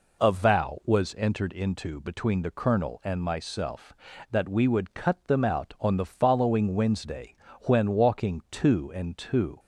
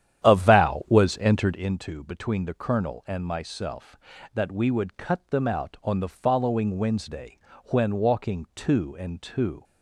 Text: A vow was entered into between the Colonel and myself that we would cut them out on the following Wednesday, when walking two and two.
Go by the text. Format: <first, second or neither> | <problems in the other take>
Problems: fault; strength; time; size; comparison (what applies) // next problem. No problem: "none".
first | starts louder than the rest; strong; until 1.8 s; 10.5 dB